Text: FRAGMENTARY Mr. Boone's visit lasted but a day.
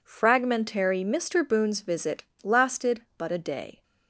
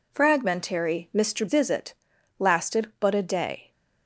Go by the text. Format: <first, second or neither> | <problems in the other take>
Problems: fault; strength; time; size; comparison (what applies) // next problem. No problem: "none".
first | skips "Boone's"; at 1.4 s // pauses between "visit" and "lasted"; at 1.9 s; 0.42 s long; slight in the first